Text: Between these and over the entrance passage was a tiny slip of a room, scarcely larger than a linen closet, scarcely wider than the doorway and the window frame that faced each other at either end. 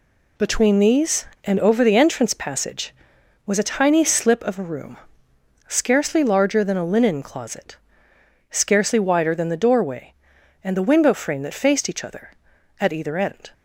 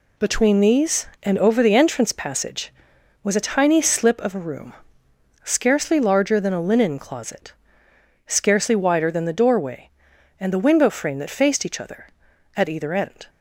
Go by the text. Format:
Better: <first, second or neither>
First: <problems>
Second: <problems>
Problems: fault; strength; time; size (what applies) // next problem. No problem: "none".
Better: neither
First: none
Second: none